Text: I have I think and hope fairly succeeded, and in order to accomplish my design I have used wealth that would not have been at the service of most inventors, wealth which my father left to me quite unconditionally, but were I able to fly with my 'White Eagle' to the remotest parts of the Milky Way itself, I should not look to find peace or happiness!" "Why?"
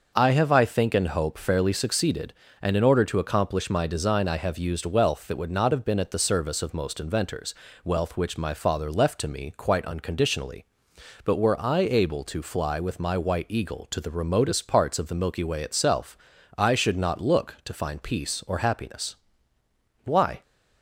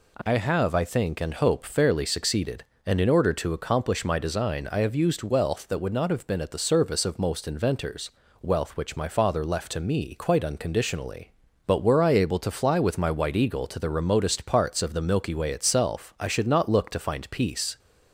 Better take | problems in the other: first | stops before "or happiness Why"; at 17.7 s

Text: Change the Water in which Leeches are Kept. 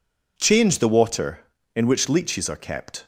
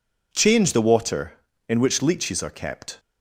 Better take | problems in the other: neither | none

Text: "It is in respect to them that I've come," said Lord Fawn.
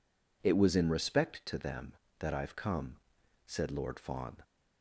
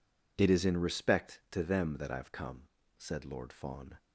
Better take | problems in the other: second | says "was" for "is"; at 0.5 s

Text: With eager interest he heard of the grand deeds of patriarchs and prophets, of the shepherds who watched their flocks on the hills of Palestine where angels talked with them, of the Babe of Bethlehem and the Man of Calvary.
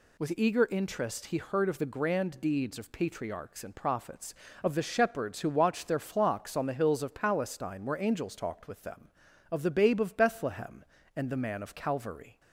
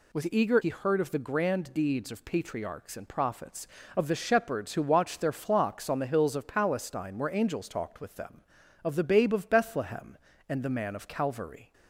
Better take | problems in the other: first | skips "interest"; at 0.6 s

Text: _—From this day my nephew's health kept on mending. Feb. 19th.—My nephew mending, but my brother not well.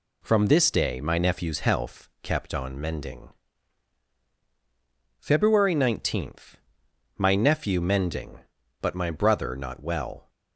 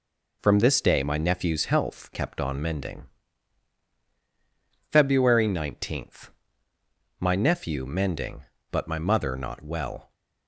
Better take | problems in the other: first | says "mother" for "brother"; at 8.9 s

